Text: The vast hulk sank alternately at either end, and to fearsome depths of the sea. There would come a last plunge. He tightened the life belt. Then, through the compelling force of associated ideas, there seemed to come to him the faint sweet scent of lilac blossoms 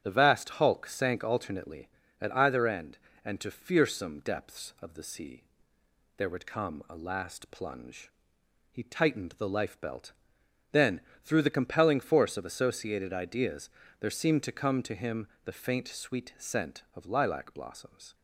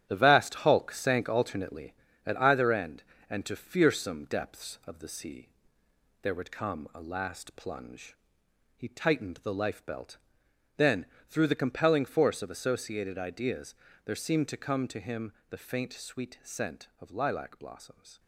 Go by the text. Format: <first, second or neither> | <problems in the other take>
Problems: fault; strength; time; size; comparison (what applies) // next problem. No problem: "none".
first | gets quieter; strong; throughout; 8 dB // starts louder than the rest; strong; until 1.1 s; 11 dB; strong in the first // pauses between "him" and "the"; slight; at 15.3 s; 0.18 s long; slight in the first